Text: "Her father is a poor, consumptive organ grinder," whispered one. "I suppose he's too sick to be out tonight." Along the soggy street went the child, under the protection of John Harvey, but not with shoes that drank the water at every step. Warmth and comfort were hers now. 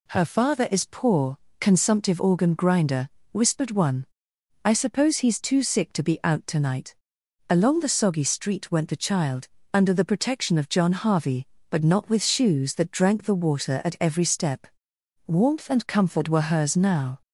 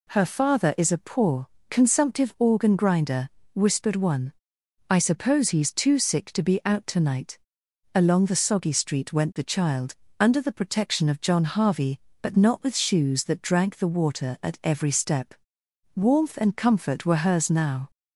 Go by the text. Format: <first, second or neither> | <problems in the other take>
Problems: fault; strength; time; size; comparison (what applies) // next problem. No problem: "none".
second | skips "a"; at 0.8 s